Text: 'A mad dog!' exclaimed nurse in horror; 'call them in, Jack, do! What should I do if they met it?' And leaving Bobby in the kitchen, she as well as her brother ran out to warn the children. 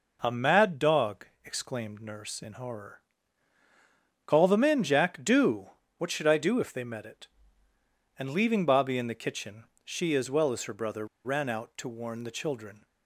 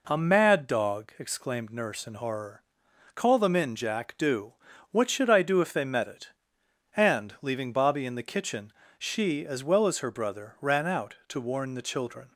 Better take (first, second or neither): second